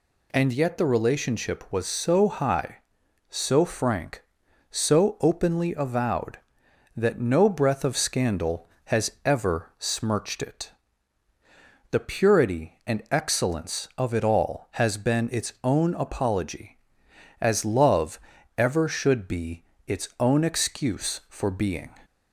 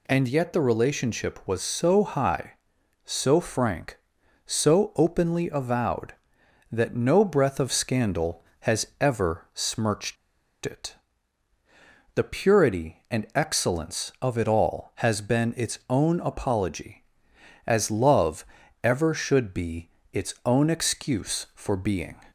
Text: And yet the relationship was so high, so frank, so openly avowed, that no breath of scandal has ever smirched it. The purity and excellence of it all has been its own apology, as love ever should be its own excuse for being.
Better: first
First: pauses between "love" and "ever"; at 18.1 s; 0.38 s long // pauses between "be" and "its"; slight; at 19.6 s; 0.22 s long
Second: pauses between "smirched" and "it"; noticeable; at 10.1 s; 0.49 s long // pauses between "love" and "ever"; at 18.4 s; 0.38 s long // pauses between "be" and "its"; slight; at 19.8 s; 0.22 s long

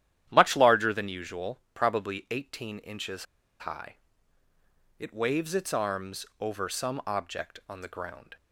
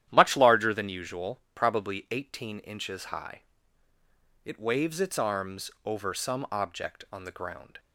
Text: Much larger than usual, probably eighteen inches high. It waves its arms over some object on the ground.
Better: second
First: starts louder than the rest; strong; until 1.3 s; 11 dB // pauses between "inches" and "high"; slight; at 3.2 s; 0.34 s long // pauses between "arms" and "over"; slight; at 6.2 s; 0.16 s long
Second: starts louder than the rest; strong; until 1.1 s; 11.5 dB // pauses between "arms" and "over"; slight; at 5.6 s; 0.16 s long

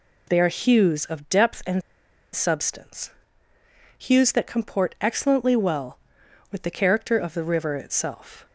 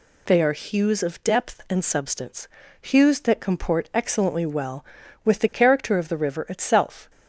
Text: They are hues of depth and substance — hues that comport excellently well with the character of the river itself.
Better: second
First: pauses between "and" and "substance"; noticeable; at 1.8 s; 0.52 s long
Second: none

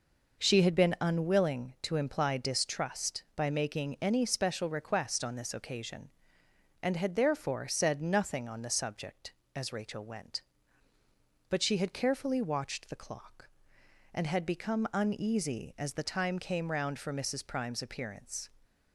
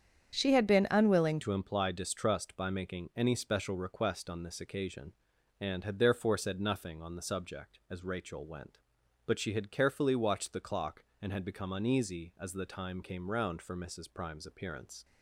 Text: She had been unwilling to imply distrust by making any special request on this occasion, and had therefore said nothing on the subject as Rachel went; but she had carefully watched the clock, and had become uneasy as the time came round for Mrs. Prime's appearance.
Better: first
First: none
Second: starts louder than the rest; strong; until 1.3 s; 8 dB // changes voice at "to"; from 1.4 s on; 13.6 s long

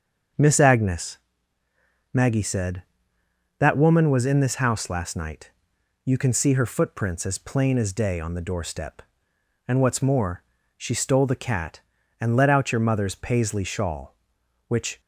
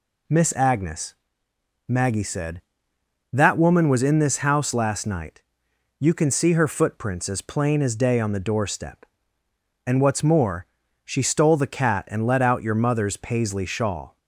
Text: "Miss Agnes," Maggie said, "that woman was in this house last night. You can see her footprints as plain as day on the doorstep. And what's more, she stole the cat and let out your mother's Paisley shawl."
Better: second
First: starts louder than the rest; until 2.3 s; 7 dB // goes on to say "Which"; slight; from 14.6 s on; 0.34 s long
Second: none

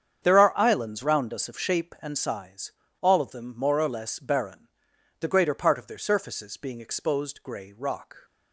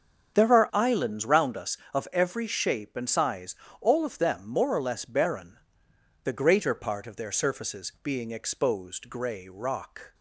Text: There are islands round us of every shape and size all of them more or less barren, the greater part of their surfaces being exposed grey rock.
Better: second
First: starts louder than the rest; strong; until 1.2 s; 8 dB // skips "every"; at 1.5 s // pauses between "size" and "all"; slight; at 2.7 s; 0.29 s long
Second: starts louder than the rest; strong; until 1.3 s; 7.5 dB // pauses between "size" and "all"; slight; at 3.5 s; 0.28 s long

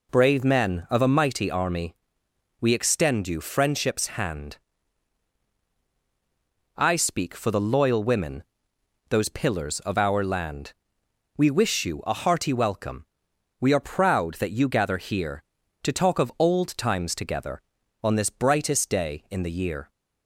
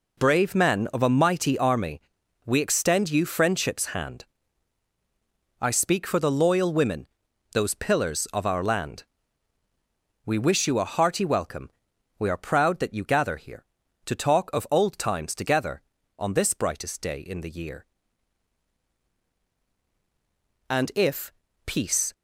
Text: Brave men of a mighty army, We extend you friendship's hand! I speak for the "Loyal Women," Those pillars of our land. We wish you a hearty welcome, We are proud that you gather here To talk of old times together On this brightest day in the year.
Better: first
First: none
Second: goes on to say "And if Peace"; from 20.6 s on; 1.4 s long

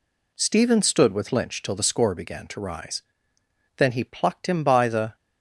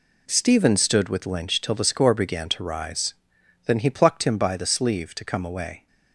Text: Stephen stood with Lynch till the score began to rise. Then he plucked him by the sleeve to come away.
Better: second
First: stops before "sleeve to come away"; at 5.1 s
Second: none

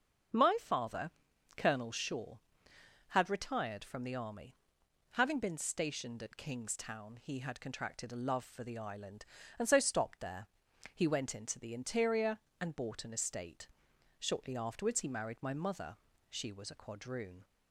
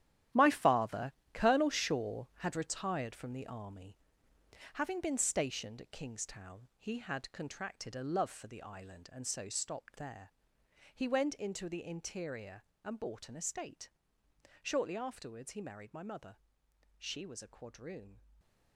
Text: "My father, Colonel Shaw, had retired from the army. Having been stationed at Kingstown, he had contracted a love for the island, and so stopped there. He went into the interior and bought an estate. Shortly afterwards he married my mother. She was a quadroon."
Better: first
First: starts louder than the rest; until 1.8 s; 6.5 dB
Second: gets quieter; strong; throughout; 12 dB // starts louder than the rest; strong; until 1.5 s; 12 dB // stays silent after the last word; slight; from 18.1 s on; 0.6 s long

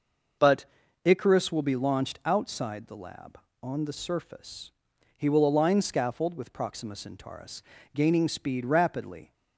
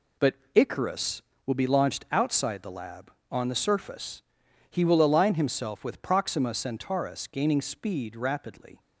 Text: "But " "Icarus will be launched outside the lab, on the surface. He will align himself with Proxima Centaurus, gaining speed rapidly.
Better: second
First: says "scaffold" for "himself"; at 5.8 s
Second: none

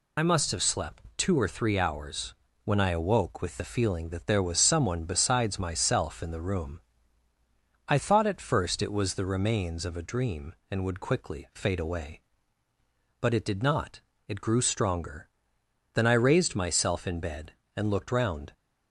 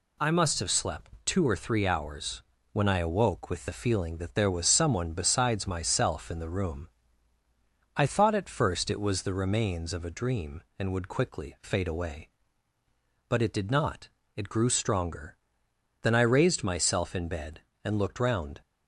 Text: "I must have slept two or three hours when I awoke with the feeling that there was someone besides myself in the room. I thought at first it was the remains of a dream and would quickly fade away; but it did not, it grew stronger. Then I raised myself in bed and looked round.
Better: second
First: loses the start of "I"; at 0.1 s; 55 ms // pauses between "hours" and "when"; slight; at 2.3 s; 0.30 s long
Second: pauses between "hours" and "when"; slight; at 2.4 s; 0.30 s long

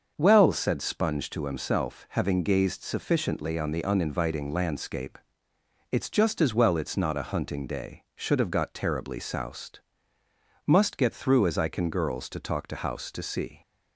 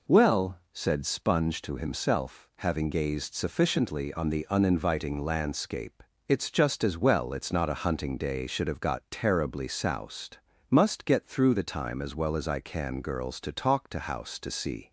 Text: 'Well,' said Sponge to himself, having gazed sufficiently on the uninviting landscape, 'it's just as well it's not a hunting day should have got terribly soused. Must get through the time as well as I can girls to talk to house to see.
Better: second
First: starts louder than the rest; until 1.1 s; 6.5 dB // skips "the time as well"; at 11.4 s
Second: none

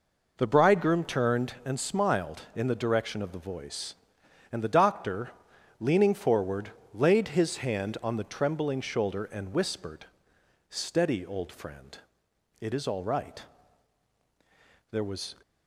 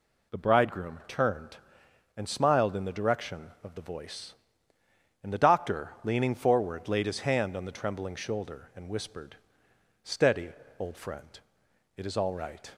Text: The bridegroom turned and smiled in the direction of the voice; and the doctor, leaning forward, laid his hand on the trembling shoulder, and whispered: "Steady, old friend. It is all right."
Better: second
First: goes on to say "There was"; slight; from 14.8 s on; 0.46 s long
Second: none

